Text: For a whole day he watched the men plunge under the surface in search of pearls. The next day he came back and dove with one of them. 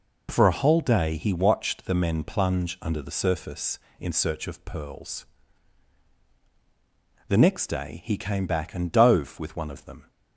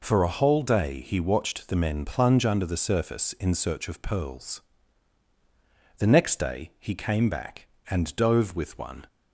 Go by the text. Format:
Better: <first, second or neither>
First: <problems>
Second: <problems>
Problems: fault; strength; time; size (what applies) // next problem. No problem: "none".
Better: first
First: none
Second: stops before "of them"; at 9.0 s